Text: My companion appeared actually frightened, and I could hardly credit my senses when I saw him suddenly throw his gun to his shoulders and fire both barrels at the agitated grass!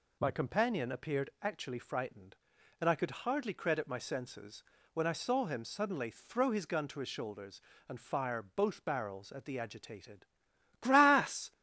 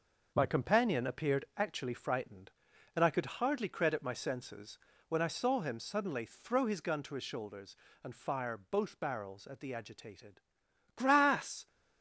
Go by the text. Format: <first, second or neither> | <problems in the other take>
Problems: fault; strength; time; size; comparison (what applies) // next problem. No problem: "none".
first | gets quieter; strong; throughout; 7.5 dB // pauses between "senses" and "when"; slight; at 4.7 s; 0.30 s long; slight in the first // pauses between "agitated" and "grass"; noticeable; at 10.4 s; 0.54 s long; noticeable in the first